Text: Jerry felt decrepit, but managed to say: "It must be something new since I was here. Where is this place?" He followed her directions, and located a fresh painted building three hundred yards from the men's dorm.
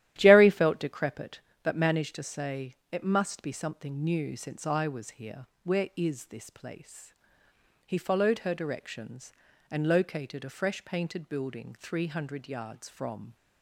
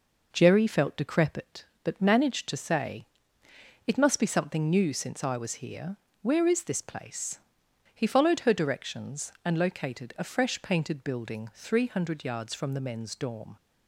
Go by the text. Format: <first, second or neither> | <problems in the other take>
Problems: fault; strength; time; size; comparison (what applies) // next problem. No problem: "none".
second | starts louder than the rest; strong; until 1.1 s; 13.5 dB // stops before "the men's dorm"; at 13.3 s